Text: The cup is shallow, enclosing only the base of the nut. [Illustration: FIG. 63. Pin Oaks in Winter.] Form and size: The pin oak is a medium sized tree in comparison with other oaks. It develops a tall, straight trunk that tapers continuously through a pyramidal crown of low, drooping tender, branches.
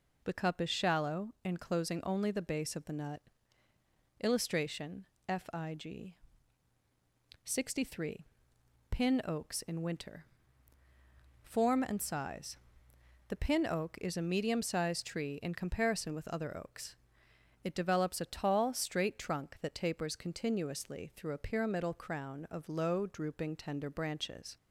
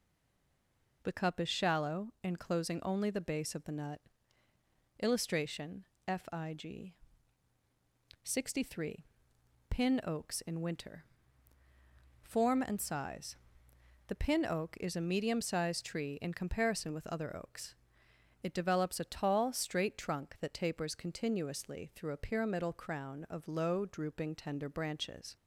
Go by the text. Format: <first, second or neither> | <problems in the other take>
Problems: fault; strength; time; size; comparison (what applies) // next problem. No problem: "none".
first | stays silent before the first word; until 1.0 s; 1.0 s long